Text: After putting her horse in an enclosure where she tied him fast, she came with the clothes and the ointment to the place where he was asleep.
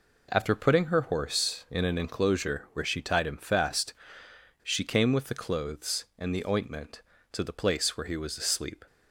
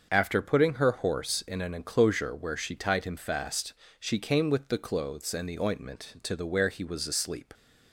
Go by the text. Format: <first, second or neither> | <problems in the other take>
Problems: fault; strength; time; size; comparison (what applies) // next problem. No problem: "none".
first | starts louder than the rest; until 1.1 s; 6.5 dB // skips "place"; at 6.4 s